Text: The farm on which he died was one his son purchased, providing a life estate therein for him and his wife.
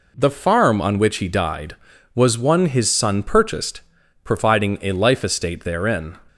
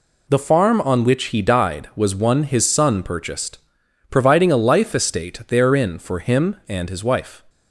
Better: second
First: stops before "for him and his wife"; at 6.2 s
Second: none

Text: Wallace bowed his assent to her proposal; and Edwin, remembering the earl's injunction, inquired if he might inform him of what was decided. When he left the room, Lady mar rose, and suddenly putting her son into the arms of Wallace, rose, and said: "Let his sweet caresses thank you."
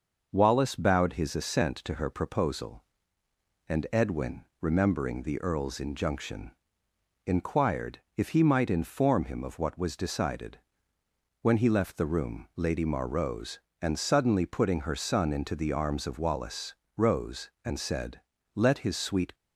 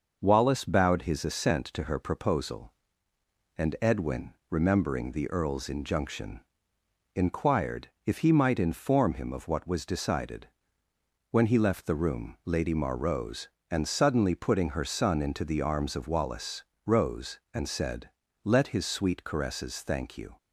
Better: second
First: pauses between "inquired" and "if"; slight; at 7.9 s; 0.16 s long // stops before "caresses thank you"; at 19.3 s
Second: pauses between "inquired" and "if"; slight; at 7.8 s; 0.16 s long

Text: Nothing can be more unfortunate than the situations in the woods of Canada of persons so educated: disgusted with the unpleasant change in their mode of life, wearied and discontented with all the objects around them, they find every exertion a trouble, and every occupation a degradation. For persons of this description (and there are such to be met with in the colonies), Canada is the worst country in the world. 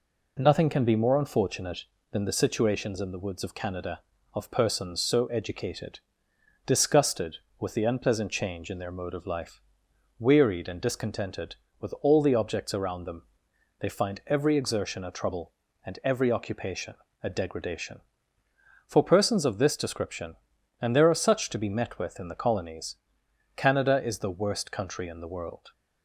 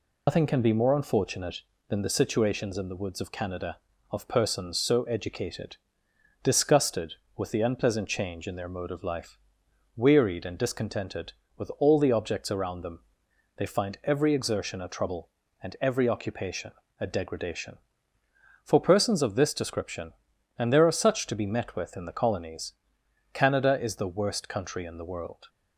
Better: first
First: pauses between "occupation" and "a"; slight; at 16.9 s; 0.30 s long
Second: loses the start of "Nothing"; at 0.2 s; 135 ms // pauses between "occupation" and "a"; slight; at 16.7 s; 0.30 s long

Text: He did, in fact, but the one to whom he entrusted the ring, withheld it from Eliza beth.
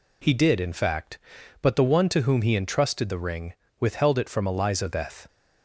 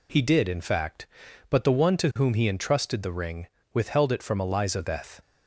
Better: neither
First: none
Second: none

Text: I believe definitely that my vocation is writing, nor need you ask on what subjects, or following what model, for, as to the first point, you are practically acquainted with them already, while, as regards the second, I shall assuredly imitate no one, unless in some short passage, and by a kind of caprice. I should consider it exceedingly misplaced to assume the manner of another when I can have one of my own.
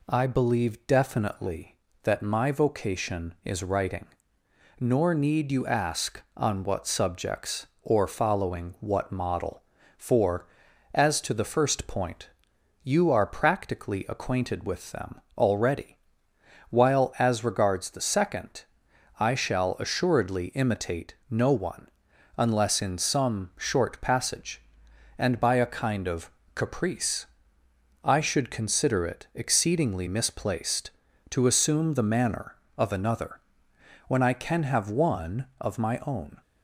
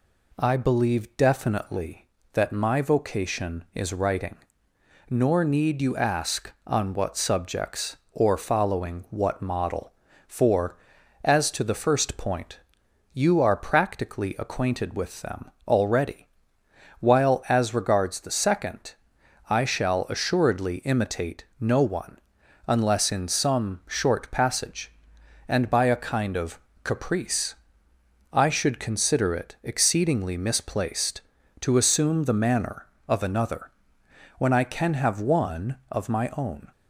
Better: neither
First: pauses between "them" and "already"; slight; at 15.2 s; 0.16 s long // pauses between "imitate" and "no"; slight; at 21.1 s; 0.16 s long // pauses between "of" and "caprice"; slight; at 26.2 s; 0.28 s long // pauses between "another" and "when"; noticeable; at 33.4 s; 0.68 s long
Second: pauses between "them" and "already"; slight; at 15.5 s; 0.16 s long // pauses between "imitate" and "no"; slight; at 21.4 s; 0.16 s long // pauses between "of" and "caprice"; slight; at 26.5 s; 0.28 s long // pauses between "another" and "when"; noticeable; at 33.7 s; 0.68 s long

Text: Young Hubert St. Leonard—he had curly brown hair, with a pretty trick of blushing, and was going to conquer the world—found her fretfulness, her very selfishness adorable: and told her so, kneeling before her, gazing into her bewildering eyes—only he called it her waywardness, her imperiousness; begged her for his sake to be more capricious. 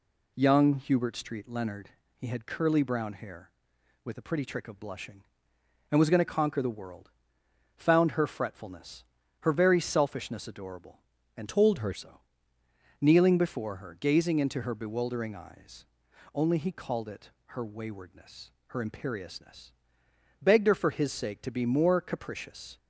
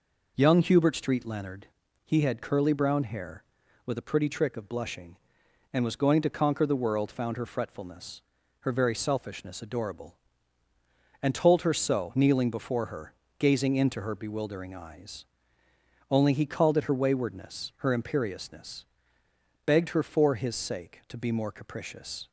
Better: second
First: changes voice from "told" to "her"; from 11.4 to 11.9 s; 0.5 s long // pauses between "it" and "her"; slight; at 17.2 s; 0.18 s long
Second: none

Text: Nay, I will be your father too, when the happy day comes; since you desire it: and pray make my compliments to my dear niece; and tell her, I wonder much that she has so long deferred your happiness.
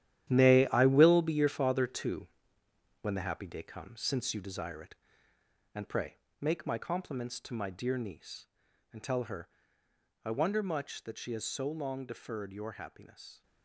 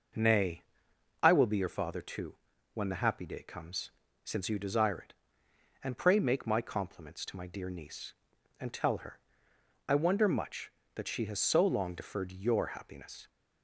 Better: second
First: gets quieter; strong; throughout; 11.5 dB // pauses between "pray" and "make"; slight; at 6.1 s; 0.20 s long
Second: none

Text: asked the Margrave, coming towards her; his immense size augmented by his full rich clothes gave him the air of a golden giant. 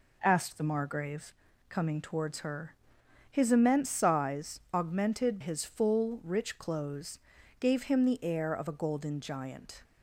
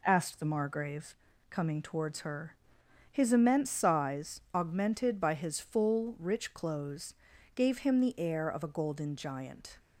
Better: second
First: skips "by"; at 5.3 s // pauses between "clothes" and "gave"; at 7.1 s; 0.40 s long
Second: pauses between "clothes" and "gave"; at 7.1 s; 0.40 s long

